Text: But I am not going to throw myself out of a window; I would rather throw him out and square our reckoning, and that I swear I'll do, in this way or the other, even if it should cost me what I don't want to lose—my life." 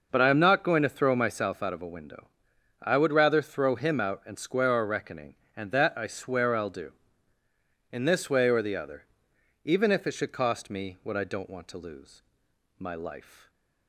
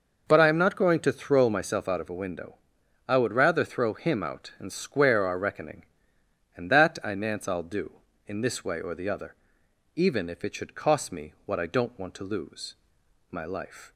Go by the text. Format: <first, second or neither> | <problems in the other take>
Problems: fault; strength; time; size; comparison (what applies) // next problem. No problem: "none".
first | says "nance" for "swear"; at 7.1 s